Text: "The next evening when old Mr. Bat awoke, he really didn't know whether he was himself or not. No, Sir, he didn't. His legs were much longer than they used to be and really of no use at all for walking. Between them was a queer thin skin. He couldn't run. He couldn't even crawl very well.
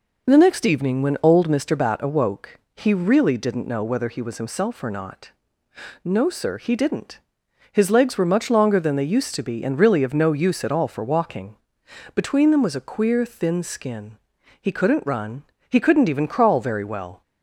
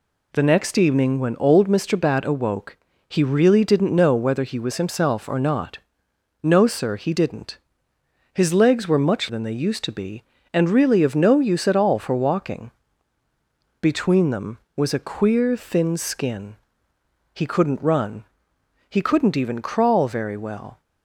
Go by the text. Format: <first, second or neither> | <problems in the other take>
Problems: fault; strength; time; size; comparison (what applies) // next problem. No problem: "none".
first | skips "longer"; at 9.2 s